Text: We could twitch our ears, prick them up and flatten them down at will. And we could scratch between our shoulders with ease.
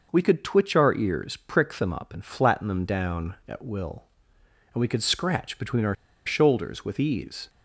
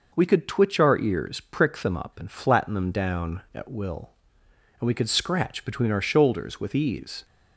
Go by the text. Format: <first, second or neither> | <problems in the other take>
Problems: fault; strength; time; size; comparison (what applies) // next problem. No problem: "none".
second | pauses between "our" and "shoulders"; slight; at 5.9 s; 0.31 s long